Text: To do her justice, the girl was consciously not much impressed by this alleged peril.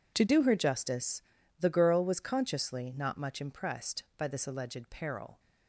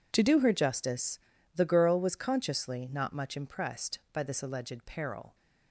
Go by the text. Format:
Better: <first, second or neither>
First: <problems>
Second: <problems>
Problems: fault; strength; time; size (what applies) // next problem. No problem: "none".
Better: neither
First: none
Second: none